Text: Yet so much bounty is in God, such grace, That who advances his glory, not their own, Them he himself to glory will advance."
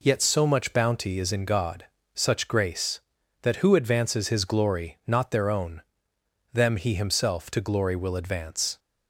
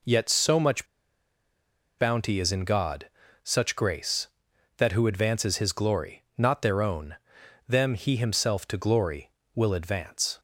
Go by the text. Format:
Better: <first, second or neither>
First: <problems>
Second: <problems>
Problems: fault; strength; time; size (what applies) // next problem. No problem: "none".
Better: first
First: none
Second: pauses between "much" and "bounty"; at 0.8 s; 1.1 s long